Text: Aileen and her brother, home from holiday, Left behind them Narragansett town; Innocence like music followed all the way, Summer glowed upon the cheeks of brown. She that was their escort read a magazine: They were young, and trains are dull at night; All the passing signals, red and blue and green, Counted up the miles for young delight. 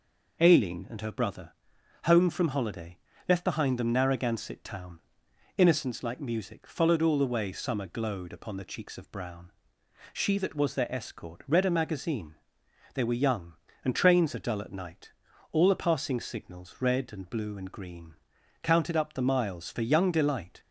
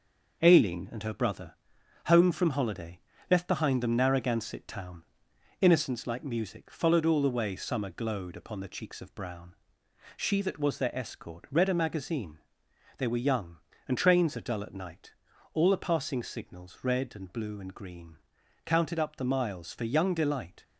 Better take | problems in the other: first | gets quieter; noticeable; throughout; 4.5 dB

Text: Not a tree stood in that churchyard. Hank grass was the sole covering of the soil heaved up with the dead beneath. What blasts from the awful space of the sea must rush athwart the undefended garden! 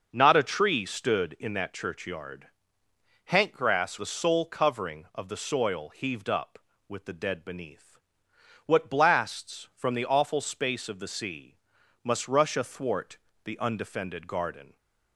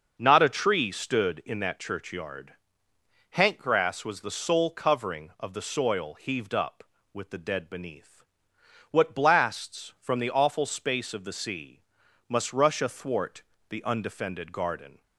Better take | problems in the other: second | starts louder than the rest; noticeable; until 1.1 s; 6 dB; noticeable in the second // skips "was"; at 3.9 s // pauses between "sea" and "must"; noticeable; at 11.5 s; 0.48 s long; noticeable in the second // pauses between "athwart" and "the"; slight; at 13.1 s; 0.28 s long; slight in the second

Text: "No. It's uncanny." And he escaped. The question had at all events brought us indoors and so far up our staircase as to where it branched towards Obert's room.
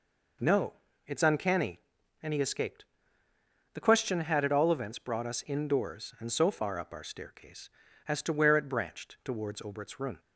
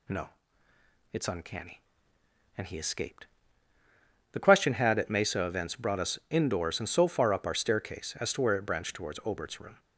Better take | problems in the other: first | says "mesa" for "all"; at 5.0 s

